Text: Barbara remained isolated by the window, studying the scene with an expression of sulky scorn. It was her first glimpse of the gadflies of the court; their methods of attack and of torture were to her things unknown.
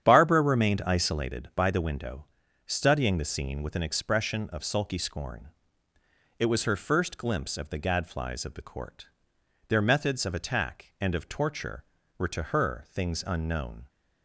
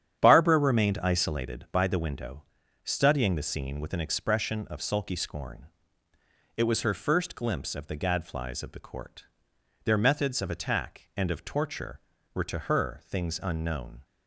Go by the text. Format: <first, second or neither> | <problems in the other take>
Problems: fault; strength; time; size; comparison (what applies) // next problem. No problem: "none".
neither | starts louder than the rest; strong; the same in both